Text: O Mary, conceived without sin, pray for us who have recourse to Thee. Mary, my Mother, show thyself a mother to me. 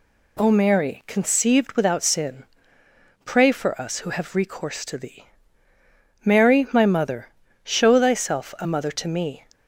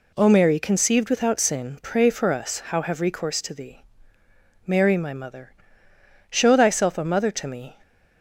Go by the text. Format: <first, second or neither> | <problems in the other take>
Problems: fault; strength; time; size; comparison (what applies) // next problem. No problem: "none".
first | says "how" for "who"; at 2.6 s